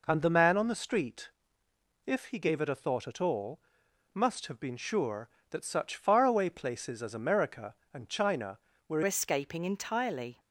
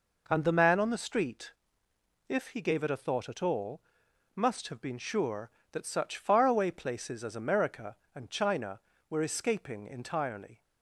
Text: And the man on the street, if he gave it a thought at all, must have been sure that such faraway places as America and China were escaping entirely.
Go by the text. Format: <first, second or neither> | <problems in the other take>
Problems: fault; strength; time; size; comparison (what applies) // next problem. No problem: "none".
second | changes voice at "escaping"; from 9.0 s on; 1.3 s long